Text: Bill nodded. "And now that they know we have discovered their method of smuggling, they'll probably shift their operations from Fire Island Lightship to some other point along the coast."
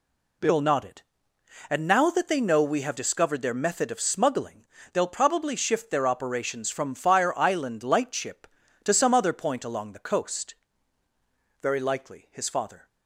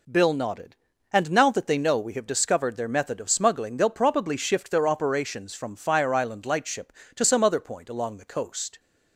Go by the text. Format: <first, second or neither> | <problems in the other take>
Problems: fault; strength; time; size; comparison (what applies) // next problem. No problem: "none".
second | goes on to say "Very likely his father"; noticeable; from 11.5 s on; 1.2 s long